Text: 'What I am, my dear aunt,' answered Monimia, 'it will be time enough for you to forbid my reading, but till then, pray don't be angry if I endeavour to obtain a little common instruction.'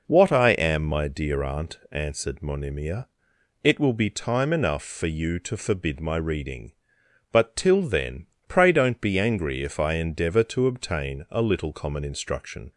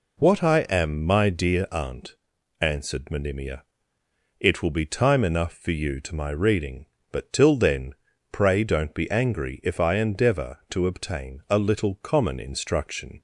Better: first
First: none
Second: skips "forbid"; at 6.1 s

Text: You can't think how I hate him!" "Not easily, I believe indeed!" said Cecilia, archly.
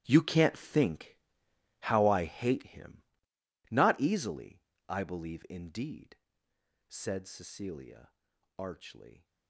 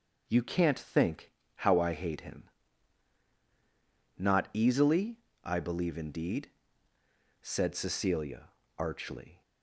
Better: second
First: gets quieter; strong; throughout; 15 dB // pauses between "think" and "how"; noticeable; at 1.1 s; 0.62 s long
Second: pauses between "think" and "how"; slight; at 1.2 s; 0.24 s long

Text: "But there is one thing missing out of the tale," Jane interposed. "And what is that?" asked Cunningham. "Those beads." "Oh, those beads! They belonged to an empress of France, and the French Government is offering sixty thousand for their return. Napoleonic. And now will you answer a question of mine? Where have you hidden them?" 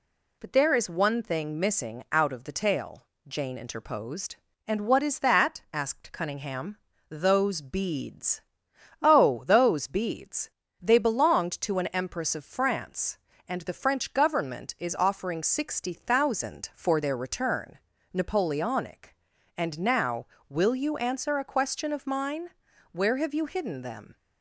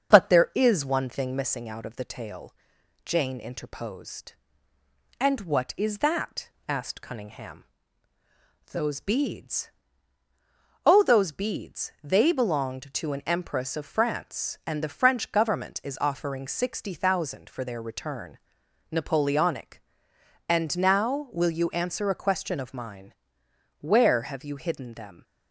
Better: first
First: none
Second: starts louder than the rest; strong; until 1.5 s; 7.5 dB

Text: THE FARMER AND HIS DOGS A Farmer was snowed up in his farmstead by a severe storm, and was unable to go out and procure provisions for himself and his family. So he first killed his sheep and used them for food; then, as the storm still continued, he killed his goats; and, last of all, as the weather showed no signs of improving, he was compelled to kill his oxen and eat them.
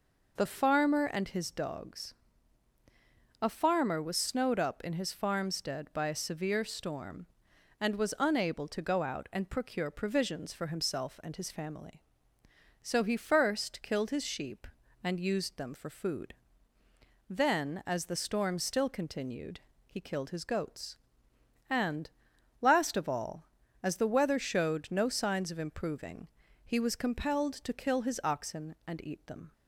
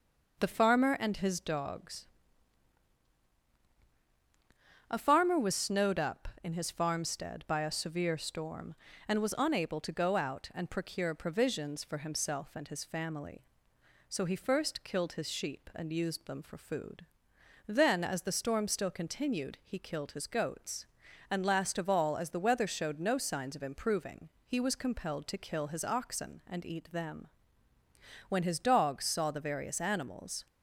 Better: first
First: pauses between "DOGS" and "A"; strong; at 2.1 s; 1.2 s long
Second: pauses between "DOGS" and "A"; strong; at 2.0 s; 2.8 s long // goes on to say "When his Dogs saw the various animals"; strong; from 28.3 s on; 2.1 s long

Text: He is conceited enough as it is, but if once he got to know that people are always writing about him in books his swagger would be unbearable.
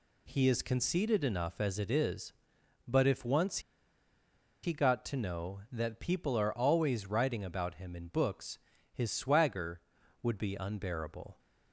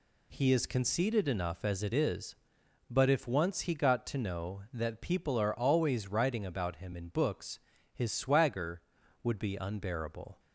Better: second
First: pauses between "once" and "he"; at 3.5 s; 1.0 s long // pauses between "books" and "his"; at 8.5 s; 0.38 s long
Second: pauses between "books" and "his"; at 7.5 s; 0.38 s long

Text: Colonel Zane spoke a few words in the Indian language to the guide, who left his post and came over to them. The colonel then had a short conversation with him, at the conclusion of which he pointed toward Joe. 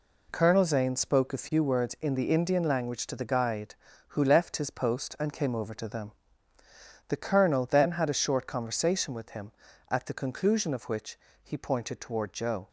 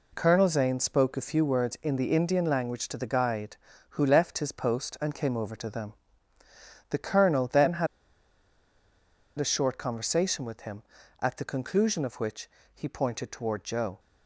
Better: first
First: pauses between "which" and "he"; slight; at 11.1 s; 0.24 s long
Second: pauses between "had" and "a"; strong; at 7.8 s; 1.5 s long // pauses between "which" and "he"; slight; at 12.4 s; 0.24 s long

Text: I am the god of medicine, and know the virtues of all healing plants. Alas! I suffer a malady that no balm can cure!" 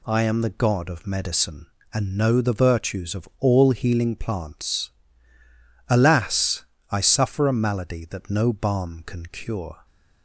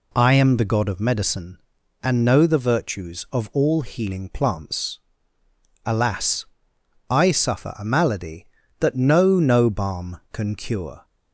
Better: first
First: none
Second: says "no" twice; at 9.3 s

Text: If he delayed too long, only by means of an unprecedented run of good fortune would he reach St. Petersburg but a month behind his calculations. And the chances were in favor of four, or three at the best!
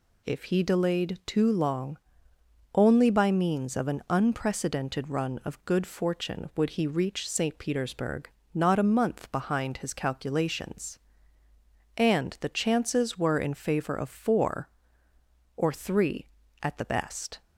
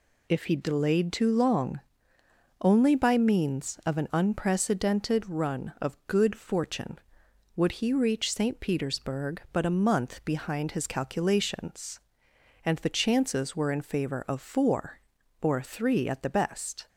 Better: second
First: says "not" for "but"; at 8.5 s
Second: none

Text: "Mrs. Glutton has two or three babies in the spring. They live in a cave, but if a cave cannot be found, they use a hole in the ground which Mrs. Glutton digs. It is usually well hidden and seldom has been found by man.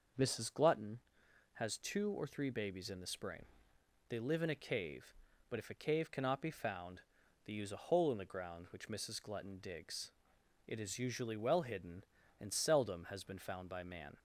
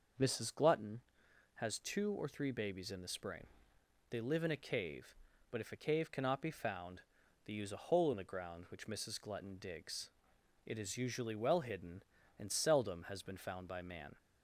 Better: neither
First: none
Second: none

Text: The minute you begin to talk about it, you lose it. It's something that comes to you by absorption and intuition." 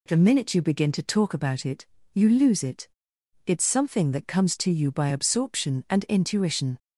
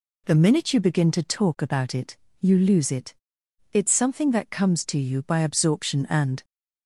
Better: first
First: none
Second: stops before "intuition"; at 6.4 s

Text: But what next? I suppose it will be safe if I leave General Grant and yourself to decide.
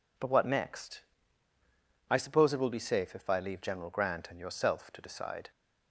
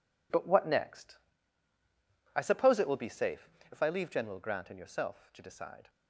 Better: first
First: none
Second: gets quieter; strong; throughout; 11.5 dB // pauses between "safe" and "if"; slight; at 3.4 s; 0.24 s long

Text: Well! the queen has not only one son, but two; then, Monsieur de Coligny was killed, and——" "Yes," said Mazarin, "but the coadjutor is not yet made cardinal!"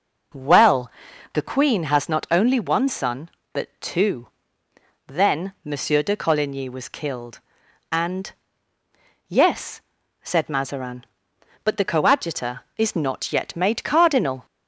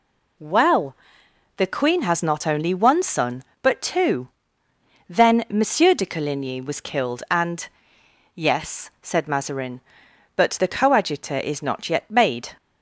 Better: first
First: none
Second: stops before "cardinal"; at 12.5 s

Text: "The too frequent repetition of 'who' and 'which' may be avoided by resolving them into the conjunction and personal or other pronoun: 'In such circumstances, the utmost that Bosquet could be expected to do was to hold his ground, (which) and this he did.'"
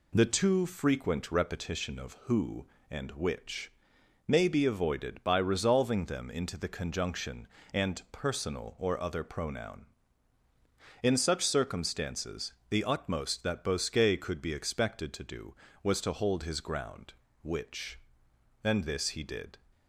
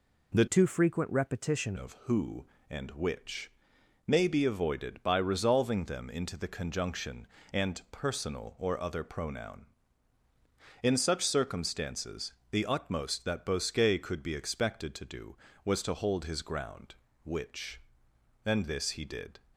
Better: first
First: pauses between "which" and "may"; noticeable; at 3.7 s; 0.56 s long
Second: changes voice from "too" to "repetition"; from 0.4 to 1.7 s; 1.3 s long // pauses between "which" and "may"; noticeable; at 3.5 s; 0.56 s long

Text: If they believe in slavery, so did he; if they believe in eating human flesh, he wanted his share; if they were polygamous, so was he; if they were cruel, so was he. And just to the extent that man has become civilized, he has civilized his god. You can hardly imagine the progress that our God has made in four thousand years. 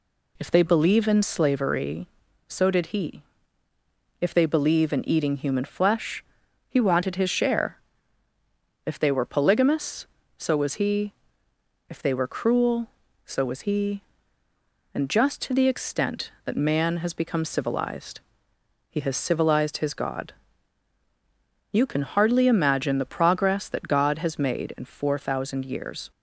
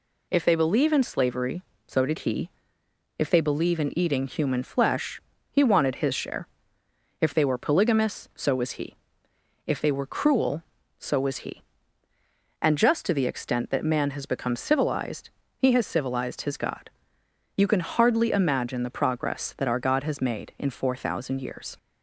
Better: second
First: skips "our"; at 23.8 s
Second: none

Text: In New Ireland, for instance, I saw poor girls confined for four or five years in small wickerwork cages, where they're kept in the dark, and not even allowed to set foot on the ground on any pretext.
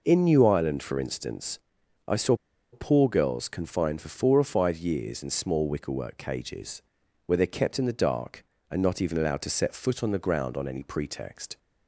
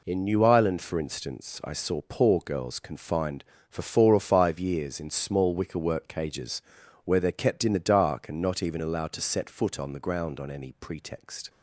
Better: second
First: pauses between "saw" and "poor"; at 2.3 s; 0.37 s long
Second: none

